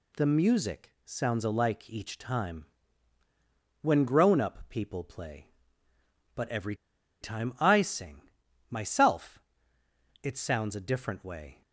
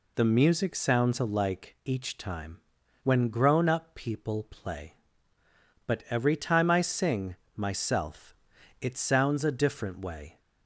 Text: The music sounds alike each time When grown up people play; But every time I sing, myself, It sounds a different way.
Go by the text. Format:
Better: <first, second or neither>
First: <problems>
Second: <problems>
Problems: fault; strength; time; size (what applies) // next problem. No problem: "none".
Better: second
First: pauses between "music" and "sounds"; slight; at 0.9 s; 0.16 s long // pauses between "time" and "When"; at 2.6 s; 1.1 s long // pauses between "every" and "time"; noticeable; at 6.7 s; 0.46 s long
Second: pauses between "time" and "When"; noticeable; at 2.5 s; 0.48 s long